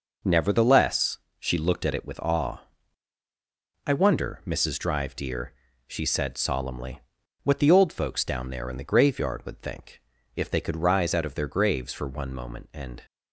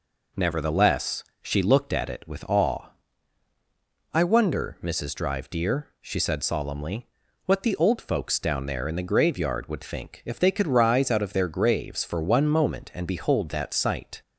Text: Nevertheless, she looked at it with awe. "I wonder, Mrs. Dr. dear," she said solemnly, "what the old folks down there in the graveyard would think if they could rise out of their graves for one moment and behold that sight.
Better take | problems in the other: second | pauses between "think" and "if"; slight; at 10.0 s; 0.32 s long // stops before "behold that sight"; at 13.0 s

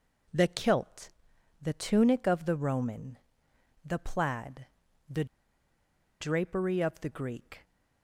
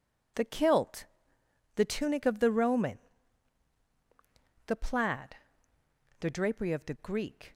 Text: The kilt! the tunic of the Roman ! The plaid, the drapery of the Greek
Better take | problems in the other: second | pauses between "the" and "drapery"; noticeable; at 5.2 s; 0.96 s long

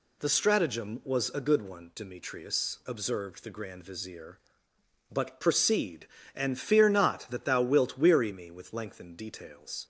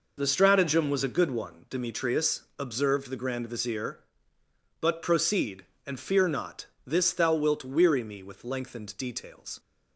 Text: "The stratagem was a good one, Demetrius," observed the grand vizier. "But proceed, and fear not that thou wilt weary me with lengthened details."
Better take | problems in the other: first | says "this" for "that"; at 6.8 s

